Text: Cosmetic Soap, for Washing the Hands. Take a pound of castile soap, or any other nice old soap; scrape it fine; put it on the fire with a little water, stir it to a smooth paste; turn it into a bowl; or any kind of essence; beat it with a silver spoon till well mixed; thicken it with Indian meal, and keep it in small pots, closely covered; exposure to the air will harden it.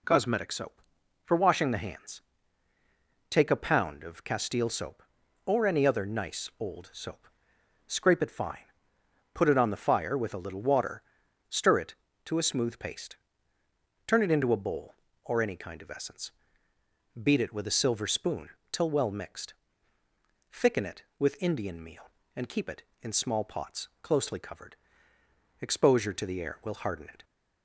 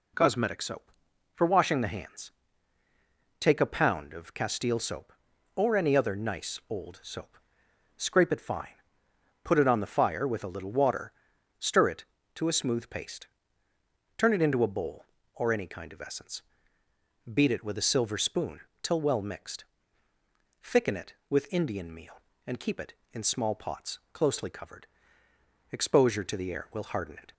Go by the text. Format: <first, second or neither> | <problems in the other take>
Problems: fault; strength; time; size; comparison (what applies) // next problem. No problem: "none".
neither | pauses between "spoon" and "till"; slight; the same in both